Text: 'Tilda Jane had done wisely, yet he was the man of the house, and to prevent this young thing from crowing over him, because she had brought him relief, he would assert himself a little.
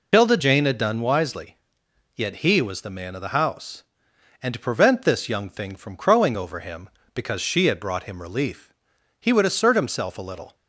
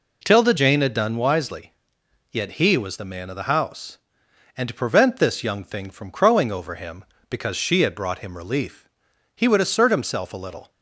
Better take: second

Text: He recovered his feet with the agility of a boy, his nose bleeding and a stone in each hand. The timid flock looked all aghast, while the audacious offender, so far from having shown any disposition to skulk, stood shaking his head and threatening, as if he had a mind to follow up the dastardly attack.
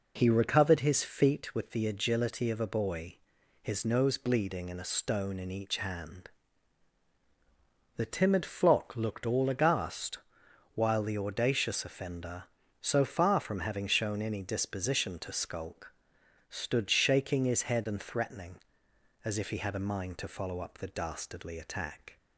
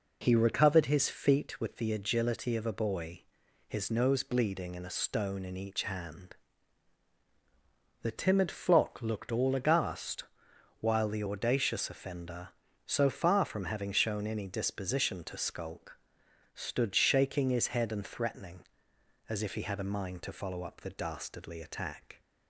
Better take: neither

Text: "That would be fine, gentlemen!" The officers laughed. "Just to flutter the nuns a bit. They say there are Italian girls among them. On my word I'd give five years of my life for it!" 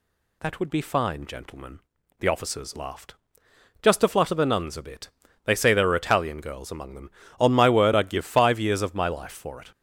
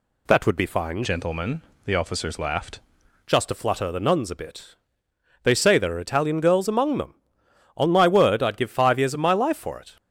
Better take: first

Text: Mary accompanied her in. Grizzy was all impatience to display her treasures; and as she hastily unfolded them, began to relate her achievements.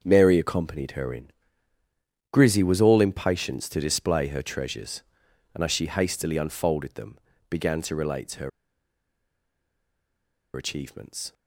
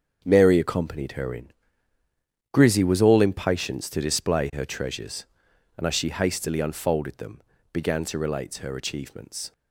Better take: second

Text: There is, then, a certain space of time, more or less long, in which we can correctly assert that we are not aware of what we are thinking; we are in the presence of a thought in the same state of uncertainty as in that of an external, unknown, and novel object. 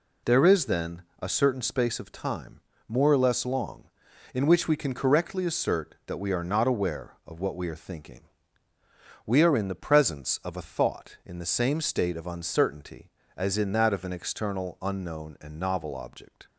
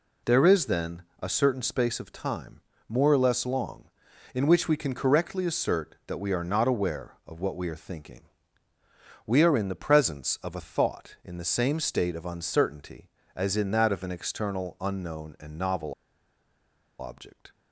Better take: first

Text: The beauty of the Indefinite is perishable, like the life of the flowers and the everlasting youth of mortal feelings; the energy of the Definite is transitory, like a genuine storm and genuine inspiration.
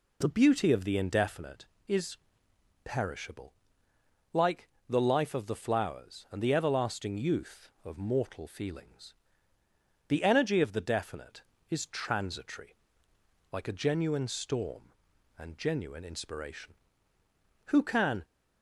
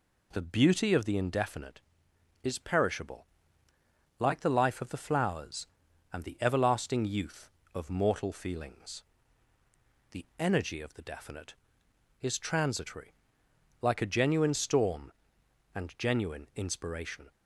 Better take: second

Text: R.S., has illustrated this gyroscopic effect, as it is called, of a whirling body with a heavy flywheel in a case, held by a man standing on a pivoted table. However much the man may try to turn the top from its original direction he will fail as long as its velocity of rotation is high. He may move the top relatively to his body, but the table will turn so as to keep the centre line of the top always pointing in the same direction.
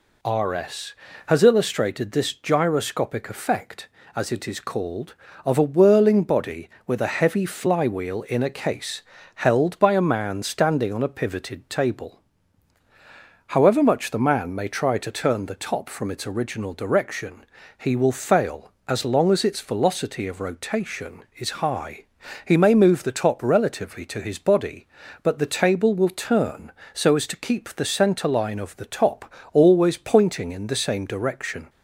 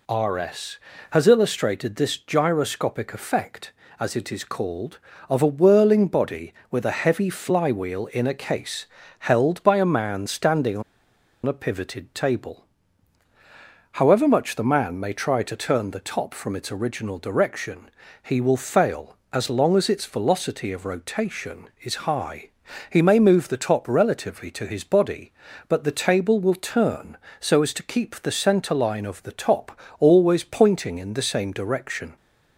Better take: first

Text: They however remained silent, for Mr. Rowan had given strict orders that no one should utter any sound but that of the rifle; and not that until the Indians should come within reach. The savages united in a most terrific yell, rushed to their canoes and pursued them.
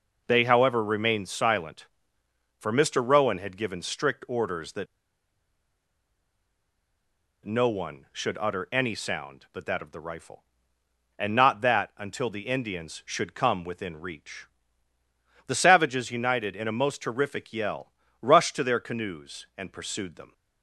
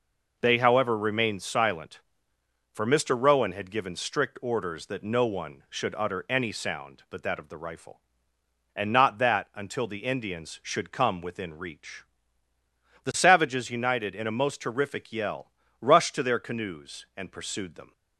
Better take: second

